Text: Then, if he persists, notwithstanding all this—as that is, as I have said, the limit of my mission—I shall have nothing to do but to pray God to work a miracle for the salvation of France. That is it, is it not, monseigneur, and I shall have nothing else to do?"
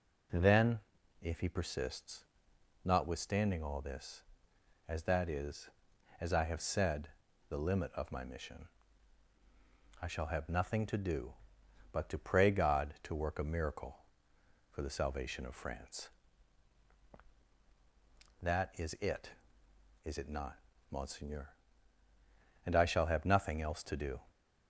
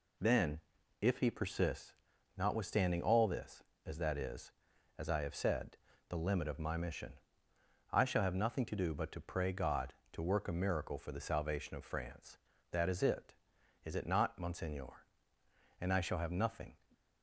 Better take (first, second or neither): first